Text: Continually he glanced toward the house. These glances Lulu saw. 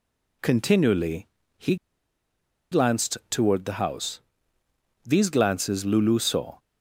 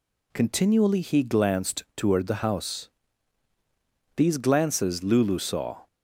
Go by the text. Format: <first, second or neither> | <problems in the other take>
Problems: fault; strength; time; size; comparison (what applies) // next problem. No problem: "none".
second | pauses between "Continually" and "he"; slight; at 1.2 s; 0.30 s long // pauses between "he" and "glanced"; noticeable; at 1.7 s; 0.96 s long